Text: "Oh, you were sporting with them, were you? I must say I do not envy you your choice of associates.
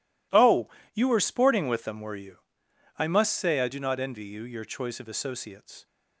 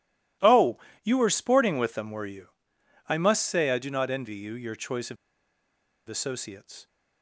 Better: first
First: none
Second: pauses between "of" and "associates"; noticeable; at 5.1 s; 0.92 s long

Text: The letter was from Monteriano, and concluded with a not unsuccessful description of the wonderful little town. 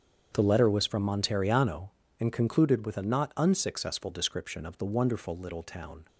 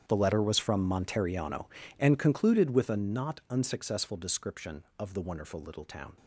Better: first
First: starts louder than the rest; strong; until 1.3 s; 7.5 dB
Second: gets quieter; strong; throughout; 17.5 dB // starts louder than the rest; strong; until 1.0 s; 9 dB

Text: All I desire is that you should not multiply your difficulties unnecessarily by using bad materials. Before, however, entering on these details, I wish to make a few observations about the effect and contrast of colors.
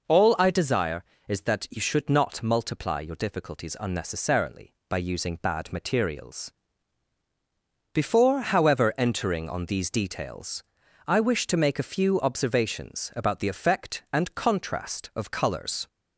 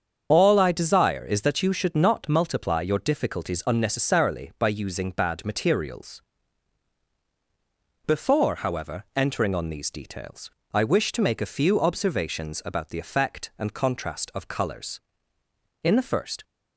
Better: first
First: none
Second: starts louder than the rest; strong; until 1.3 s; 7.5 dB // goes on to say "In the first"; from 15.8 s on; 0.60 s long

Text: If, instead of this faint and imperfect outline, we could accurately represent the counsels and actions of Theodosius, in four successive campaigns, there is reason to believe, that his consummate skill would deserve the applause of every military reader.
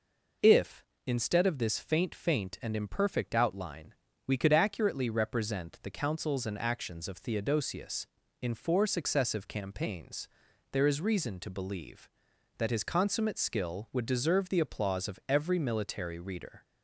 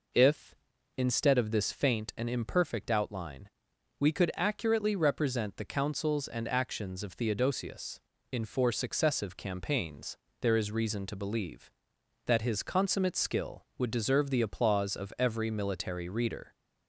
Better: second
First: says "faint" twice; at 2.1 s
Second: none

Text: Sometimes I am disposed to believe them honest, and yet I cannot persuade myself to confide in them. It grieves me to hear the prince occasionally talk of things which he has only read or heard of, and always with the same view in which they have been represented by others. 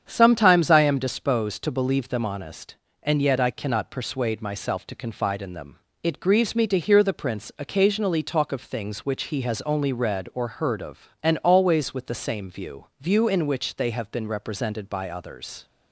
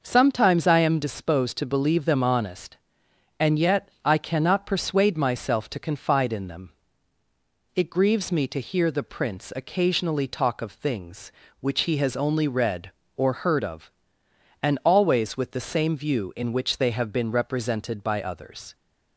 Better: second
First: starts louder than the rest; strong; until 1.0 s; 8 dB // says "view" twice; at 12.9 s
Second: none

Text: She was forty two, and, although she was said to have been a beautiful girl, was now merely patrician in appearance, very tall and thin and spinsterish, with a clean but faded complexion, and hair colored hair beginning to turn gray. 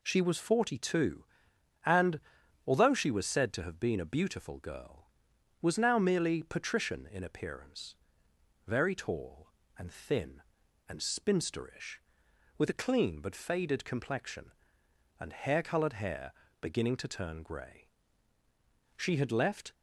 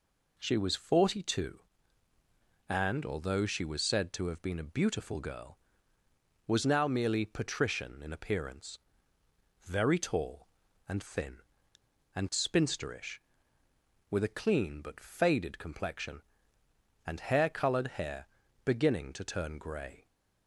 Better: second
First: pauses between "hair" and "beginning"; slight; at 16.3 s; 0.28 s long // goes on to say "She had left"; noticeable; from 18.9 s on; 0.76 s long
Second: pauses between "hair" and "beginning"; at 18.2 s; 0.38 s long

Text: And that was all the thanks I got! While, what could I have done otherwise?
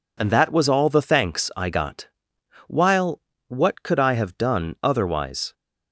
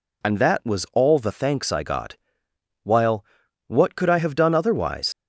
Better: first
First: none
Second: leaves "otherwise" unfinished; at 5.1 s; 75 ms

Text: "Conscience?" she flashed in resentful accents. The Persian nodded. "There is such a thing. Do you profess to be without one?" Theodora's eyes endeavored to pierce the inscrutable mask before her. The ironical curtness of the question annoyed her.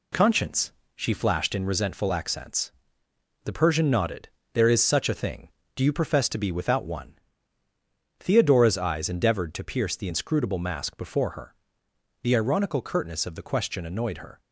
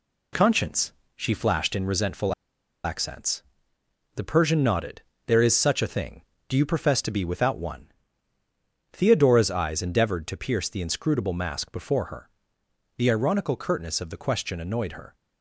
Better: first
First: none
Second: pauses between "resentful" and "accents"; noticeable; at 2.3 s; 0.50 s long

